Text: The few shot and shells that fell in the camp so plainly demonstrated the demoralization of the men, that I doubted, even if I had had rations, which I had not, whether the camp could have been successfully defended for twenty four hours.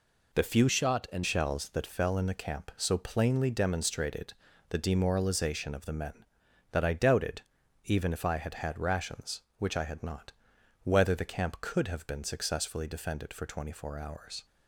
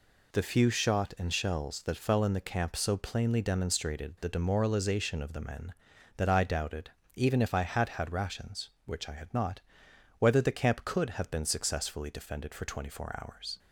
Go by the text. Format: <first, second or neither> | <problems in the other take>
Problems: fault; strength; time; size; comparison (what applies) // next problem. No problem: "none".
second | changes voice from "shot" to "and"; from 0.6 to 1.2 s; 0.6 s long // pauses between "demonstrated" and "the"; at 4.3 s; 0.38 s long